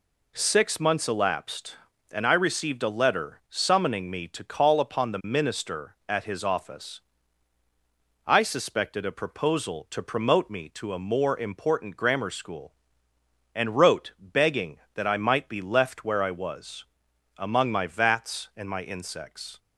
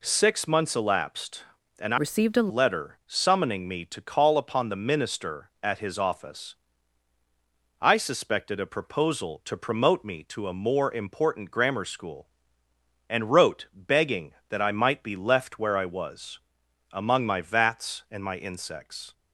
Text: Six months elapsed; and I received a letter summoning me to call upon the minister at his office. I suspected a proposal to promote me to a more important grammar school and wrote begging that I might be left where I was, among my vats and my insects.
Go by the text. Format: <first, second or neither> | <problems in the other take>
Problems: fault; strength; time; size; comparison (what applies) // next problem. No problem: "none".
first | changes voice from "received" to "a"; from 1.9 to 2.5 s; 0.6 s long